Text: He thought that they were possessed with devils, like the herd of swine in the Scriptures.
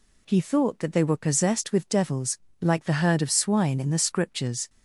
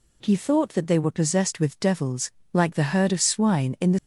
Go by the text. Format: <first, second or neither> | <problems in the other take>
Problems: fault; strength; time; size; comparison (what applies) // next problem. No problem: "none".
first | stops before "Scriptures"; at 3.9 s